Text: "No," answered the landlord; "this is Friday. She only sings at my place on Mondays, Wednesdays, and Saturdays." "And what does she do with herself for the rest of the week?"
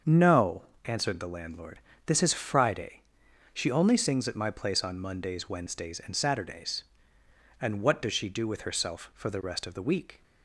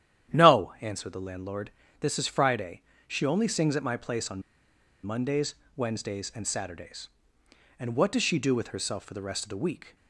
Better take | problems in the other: first | starts louder than the rest; strong; until 1.3 s; 10.5 dB; also in the first // pauses between "on" and "Mondays"; noticeable; at 4.4 s; 0.63 s long

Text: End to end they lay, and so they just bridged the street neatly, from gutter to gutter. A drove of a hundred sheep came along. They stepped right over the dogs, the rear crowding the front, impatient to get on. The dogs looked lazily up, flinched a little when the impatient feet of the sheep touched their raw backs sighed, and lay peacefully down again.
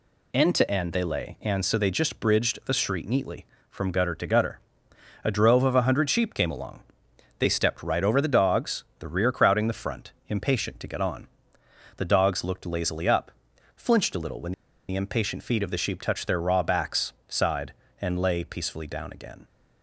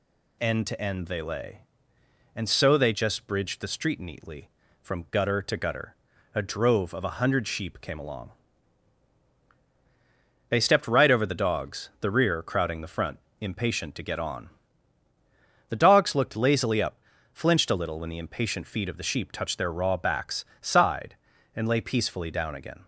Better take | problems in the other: second | pauses between "when" and "the"; slight; at 14.5 s; 0.35 s long // pauses between "backs" and "sighed"; slight; at 17.1 s; 0.16 s long; slight in the second

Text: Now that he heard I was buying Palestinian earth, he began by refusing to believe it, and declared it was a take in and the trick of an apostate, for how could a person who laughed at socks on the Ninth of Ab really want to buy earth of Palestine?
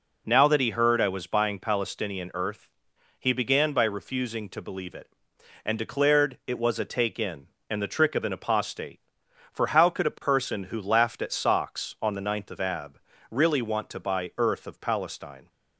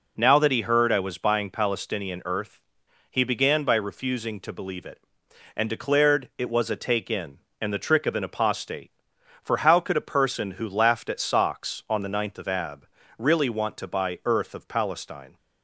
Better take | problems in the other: neither | pauses between "Ab" and "really"; slight; the same in both

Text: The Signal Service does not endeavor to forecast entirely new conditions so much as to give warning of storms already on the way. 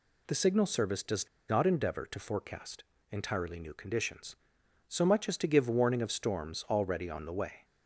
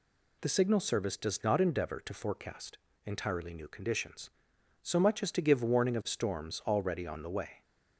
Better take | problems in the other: second | pauses between "does" and "not"; slight; at 1.2 s; 0.20 s long // pauses between "forecast" and "entirely"; slight; at 2.8 s; 0.30 s long; slight in the second

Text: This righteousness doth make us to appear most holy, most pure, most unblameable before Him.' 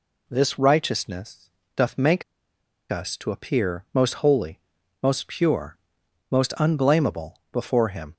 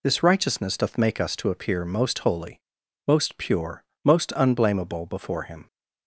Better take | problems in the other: second | pauses between "righteousness" and "doth"; slight; at 1.5 s; 0.26 s long // pauses between "make" and "us"; noticeable; at 2.2 s; 0.67 s long

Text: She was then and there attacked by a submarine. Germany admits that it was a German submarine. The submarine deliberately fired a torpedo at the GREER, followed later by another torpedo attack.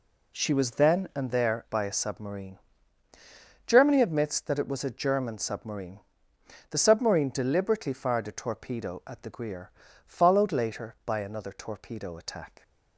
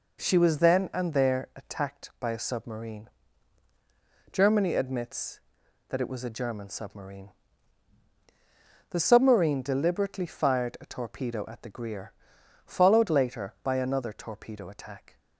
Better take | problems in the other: second | skips "attacked"; at 1.6 s

